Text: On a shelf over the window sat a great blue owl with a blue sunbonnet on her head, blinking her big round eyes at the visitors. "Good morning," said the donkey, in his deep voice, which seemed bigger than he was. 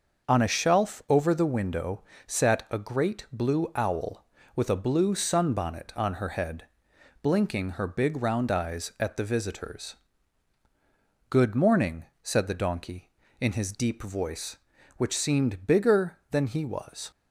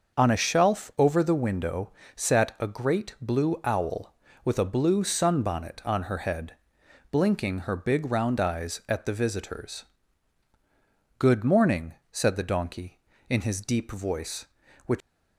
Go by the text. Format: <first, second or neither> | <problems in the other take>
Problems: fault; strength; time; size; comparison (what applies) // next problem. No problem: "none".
first | starts louder than the rest; until 1.2 s; 6 dB; also in the first // pauses between "window" and "sat"; slight; at 1.9 s; 0.24 s long; slight in the first // stops before "seemed bigger than he was"; at 15.0 s